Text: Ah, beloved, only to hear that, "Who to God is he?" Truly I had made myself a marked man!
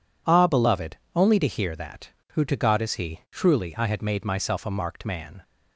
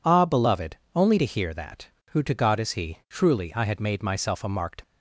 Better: first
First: none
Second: stops before "man"; at 4.8 s

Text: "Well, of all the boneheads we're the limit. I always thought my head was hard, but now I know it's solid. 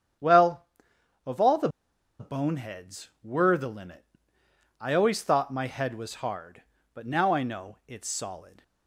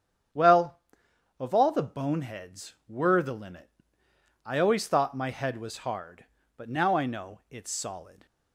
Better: second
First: starts louder than the rest; strong; until 2.3 s; 8.5 dB // pauses between "the" and "boneheads"; noticeable; at 1.6 s; 0.51 s long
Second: starts louder than the rest; strong; until 1.9 s; 8.5 dB

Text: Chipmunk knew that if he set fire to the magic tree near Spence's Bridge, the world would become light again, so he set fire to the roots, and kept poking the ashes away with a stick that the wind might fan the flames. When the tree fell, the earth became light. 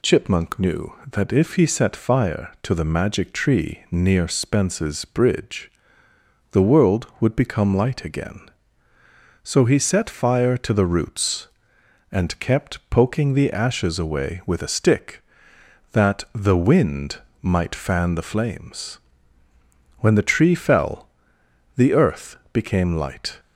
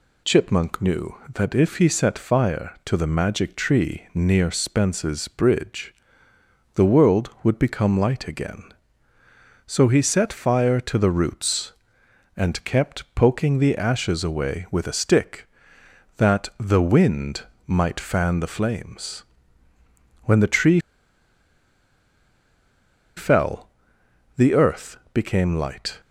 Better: first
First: pauses between "wind" and "might"; slight; at 17.1 s; 0.24 s long // pauses between "earth" and "became"; slight; at 22.3 s; 0.16 s long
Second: pauses between "wind" and "might"; slight; at 17.4 s; 0.24 s long // pauses between "tree" and "fell"; strong; at 20.7 s; 2.3 s long // pauses between "earth" and "became"; slight; at 24.9 s; 0.16 s long

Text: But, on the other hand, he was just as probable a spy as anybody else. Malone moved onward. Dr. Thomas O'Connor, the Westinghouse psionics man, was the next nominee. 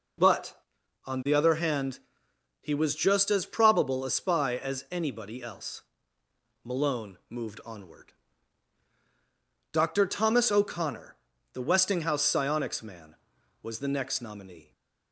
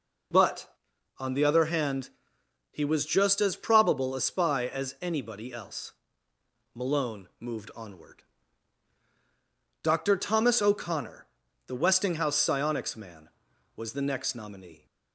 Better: neither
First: none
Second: none

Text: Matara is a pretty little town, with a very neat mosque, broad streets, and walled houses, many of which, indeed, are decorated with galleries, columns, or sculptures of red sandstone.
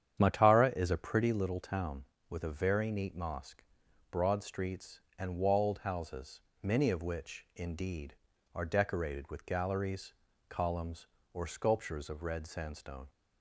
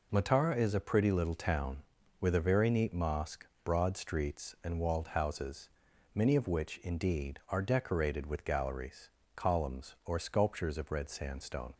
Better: second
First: starts louder than the rest; strong; until 1.3 s; 9 dB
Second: none

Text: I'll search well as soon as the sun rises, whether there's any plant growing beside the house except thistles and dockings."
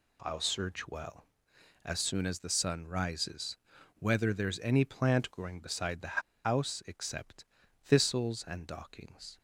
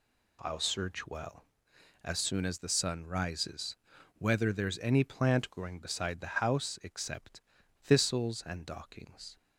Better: second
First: pauses between "the" and "house"; slight; at 6.2 s; 0.24 s long // pauses between "except" and "thistles"; slight; at 7.4 s; 0.36 s long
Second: pauses between "except" and "thistles"; at 7.4 s; 0.38 s long

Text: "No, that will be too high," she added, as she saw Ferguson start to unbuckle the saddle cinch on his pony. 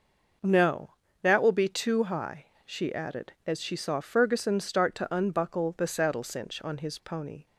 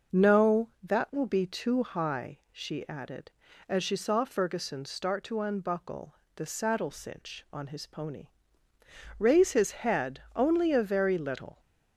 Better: first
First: none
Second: starts louder than the rest; noticeable; until 1.2 s; 6 dB // pauses between "unbuckle" and "the"; slight; at 6.1 s; 0.20 s long // goes on to say "Raise his head only a very little"; strong; from 9.1 s on; 2.4 s long

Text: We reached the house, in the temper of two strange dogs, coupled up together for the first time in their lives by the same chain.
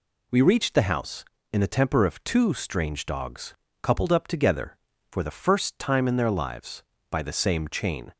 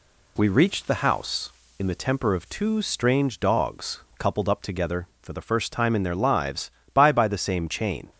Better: first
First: none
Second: says "by" twice; at 7.1 s

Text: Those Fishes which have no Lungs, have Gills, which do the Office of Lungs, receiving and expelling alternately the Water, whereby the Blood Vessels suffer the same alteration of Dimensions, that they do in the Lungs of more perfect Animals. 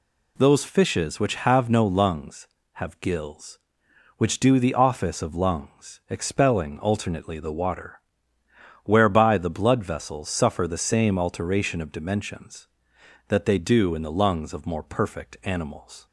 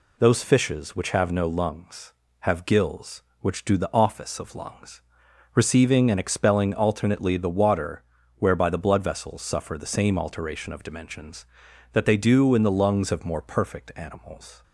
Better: second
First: skips "receiving and"; at 6.0 s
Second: none

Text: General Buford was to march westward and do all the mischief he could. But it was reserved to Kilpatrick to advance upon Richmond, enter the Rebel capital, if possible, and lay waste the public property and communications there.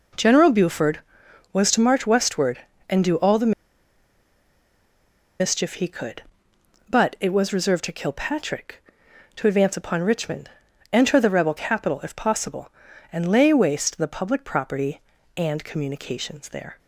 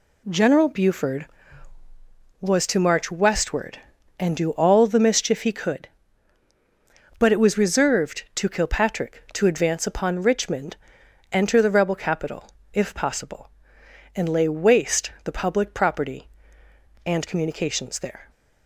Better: second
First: pauses between "the" and "mischief"; strong; at 3.5 s; 1.8 s long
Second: none

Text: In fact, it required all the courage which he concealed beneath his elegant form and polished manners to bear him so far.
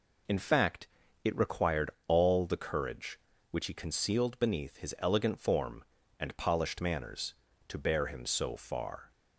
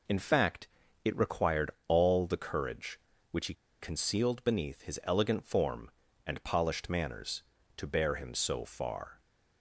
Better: first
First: pauses between "required" and "all"; slight; at 1.9 s; 0.16 s long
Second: pauses between "required" and "all"; slight; at 1.7 s; 0.16 s long // pauses between "he" and "concealed"; slight; at 3.5 s; 0.26 s long

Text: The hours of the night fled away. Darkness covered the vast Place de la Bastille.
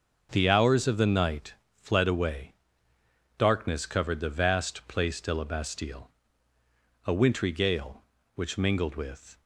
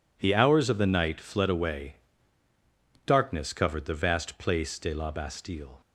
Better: second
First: starts louder than the rest; until 1.3 s; 6 dB // pauses between "night" and "fled"; slight; at 1.5 s; 0.20 s long // goes on to say "A wintry gale which mingled with"; strong; from 7.0 s on; 2.3 s long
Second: none

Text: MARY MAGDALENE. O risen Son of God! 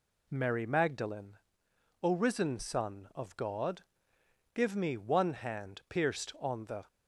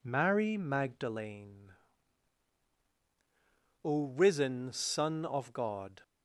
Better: second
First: goes on to say "Give me one hand pierced on the"; strong; from 4.5 s on; 2.3 s long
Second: none

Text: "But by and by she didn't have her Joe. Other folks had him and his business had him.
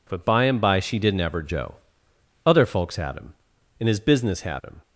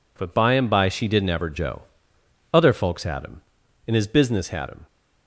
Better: neither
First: none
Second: none

